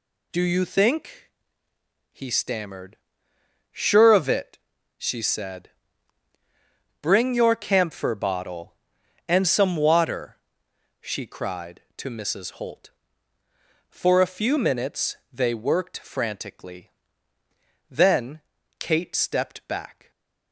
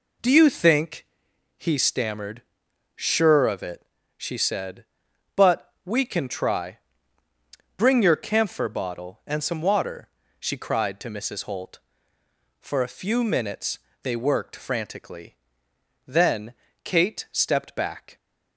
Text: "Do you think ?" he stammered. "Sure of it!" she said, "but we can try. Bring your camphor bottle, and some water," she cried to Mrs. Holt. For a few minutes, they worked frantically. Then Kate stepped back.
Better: second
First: skips "but we can try"; at 6.3 s // pauses between "Then" and "Kate"; slight; at 18.4 s; 0.36 s long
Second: pauses between "Then" and "Kate"; slight; at 16.5 s; 0.28 s long

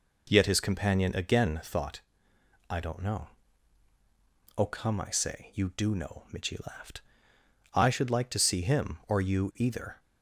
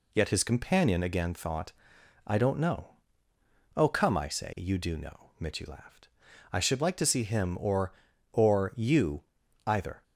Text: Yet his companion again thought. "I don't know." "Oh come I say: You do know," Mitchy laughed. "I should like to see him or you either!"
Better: first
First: none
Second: says "or" twice; at 8.3 s // pauses between "you" and "either"; at 9.2 s; 0.44 s long

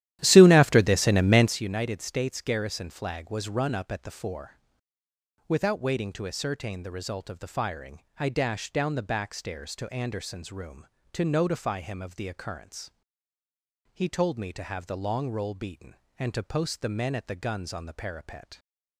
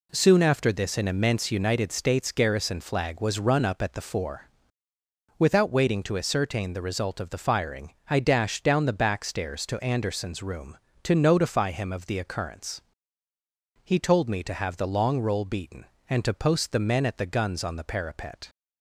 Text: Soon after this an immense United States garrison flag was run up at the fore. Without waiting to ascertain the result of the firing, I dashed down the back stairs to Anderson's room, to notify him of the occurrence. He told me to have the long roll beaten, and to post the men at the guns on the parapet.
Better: second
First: starts louder than the rest; strong; until 1.6 s; 13 dB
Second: none

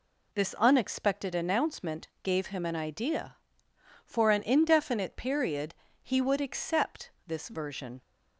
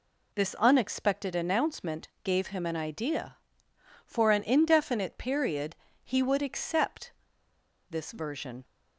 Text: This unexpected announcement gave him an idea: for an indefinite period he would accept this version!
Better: first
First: pauses between "announcement" and "gave"; slight; at 2.0 s; 0.16 s long // pauses between "period" and "he"; slight; at 5.7 s; 0.30 s long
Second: pauses between "announcement" and "gave"; slight; at 2.0 s; 0.16 s long // pauses between "period" and "he"; slight; at 5.7 s; 0.30 s long // pauses between "accept" and "this"; noticeable; at 7.1 s; 0.76 s long

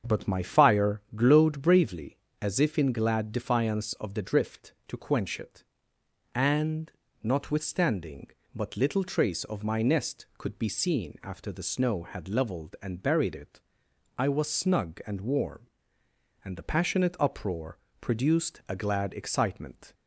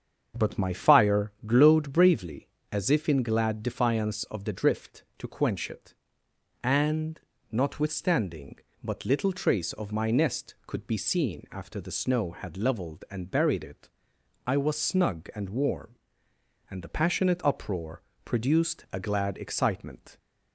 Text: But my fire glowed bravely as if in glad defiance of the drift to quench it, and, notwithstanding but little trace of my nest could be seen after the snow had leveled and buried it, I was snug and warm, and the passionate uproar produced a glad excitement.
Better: neither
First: starts louder than the rest; strong; until 1.2 s; 7 dB // pauses between "uproar" and "produced"; slight; at 17.7 s; 0.22 s long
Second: starts louder than the rest; strong; until 1.5 s; 7 dB // pauses between "uproar" and "produced"; slight; at 18.0 s; 0.22 s long

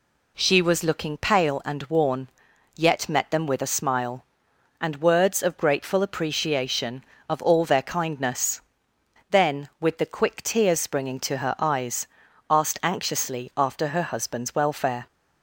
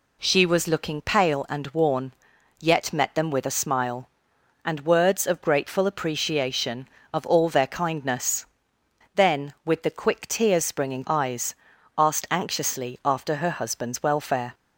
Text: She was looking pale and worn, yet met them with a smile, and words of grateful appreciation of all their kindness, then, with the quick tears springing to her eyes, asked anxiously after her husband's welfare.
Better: first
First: none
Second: skips "to her"; at 11.0 s

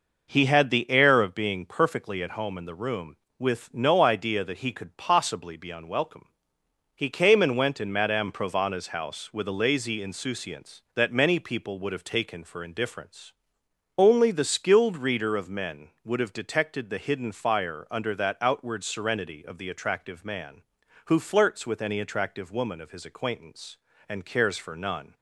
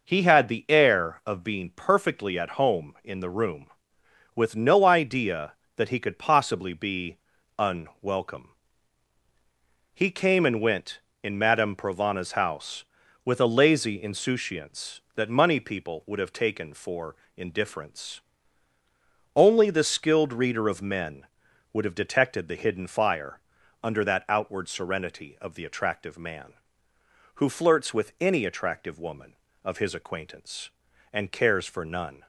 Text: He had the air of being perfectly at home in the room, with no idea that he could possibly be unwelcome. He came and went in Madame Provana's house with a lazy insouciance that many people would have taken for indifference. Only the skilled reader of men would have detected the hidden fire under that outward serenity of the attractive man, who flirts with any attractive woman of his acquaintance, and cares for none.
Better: first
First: none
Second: pauses between "be" and "unwelcome"; at 7.1 s; 0.41 s long // says "money" for "many"; at 15.2 s // pauses between "for" and "indifference"; slight; at 17.1 s; 0.20 s long // pauses between "fire" and "under"; at 23.4 s; 0.42 s long

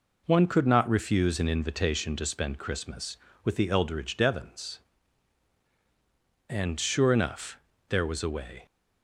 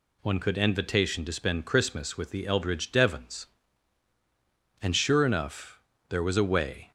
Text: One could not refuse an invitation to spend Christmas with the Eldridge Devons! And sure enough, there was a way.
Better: first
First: none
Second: skips "not refuse an"; at 0.5 s

